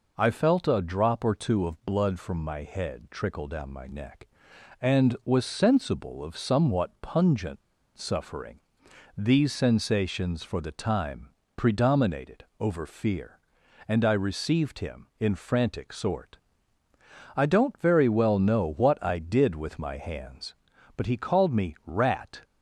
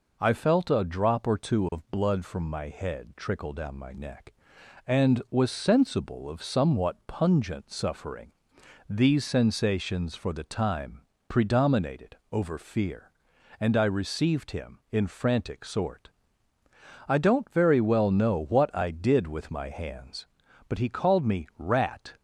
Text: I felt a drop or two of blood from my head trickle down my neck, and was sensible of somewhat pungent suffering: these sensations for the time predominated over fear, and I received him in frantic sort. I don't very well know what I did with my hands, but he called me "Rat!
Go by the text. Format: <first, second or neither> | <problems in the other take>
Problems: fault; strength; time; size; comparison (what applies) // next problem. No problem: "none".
second | pauses between "pungent" and "suffering"; at 7.6 s; 0.36 s long // pauses between "time" and "predominated"; slight; at 11.3 s; 0.26 s long; slight in the second // pauses between "predominated" and "over"; slight; at 12.4 s; 0.16 s long; slight in the second